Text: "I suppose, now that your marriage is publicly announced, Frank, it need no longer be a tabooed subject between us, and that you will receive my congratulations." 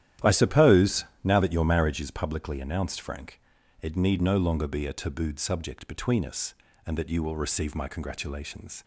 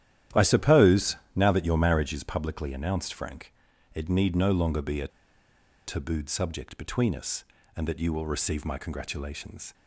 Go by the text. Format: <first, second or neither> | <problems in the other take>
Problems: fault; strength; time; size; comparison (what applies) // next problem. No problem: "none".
first | starts louder than the rest; strong; until 1.5 s; 11.5 dB; strong in the first // pauses between "a" and "tabooed"; noticeable; at 5.0 s; 0.78 s long